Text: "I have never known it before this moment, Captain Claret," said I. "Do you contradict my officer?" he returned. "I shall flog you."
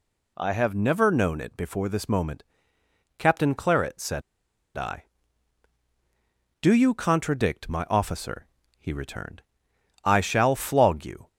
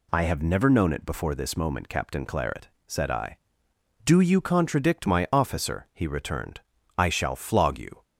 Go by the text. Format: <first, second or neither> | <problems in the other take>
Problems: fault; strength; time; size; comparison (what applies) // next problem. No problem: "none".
second | pauses between "said" and "I"; noticeable; at 4.2 s; 0.55 s long